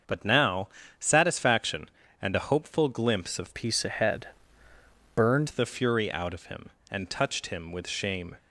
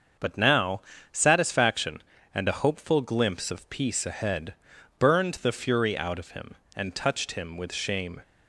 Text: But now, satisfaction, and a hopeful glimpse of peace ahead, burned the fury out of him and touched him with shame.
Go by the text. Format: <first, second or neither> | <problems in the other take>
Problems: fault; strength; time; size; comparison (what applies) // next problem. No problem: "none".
second | starts louder than the rest; until 1.3 s; 6 dB; also in the second // changes voice from "peace" to "burned"; from 3.5 to 5.4 s; 1.9 s long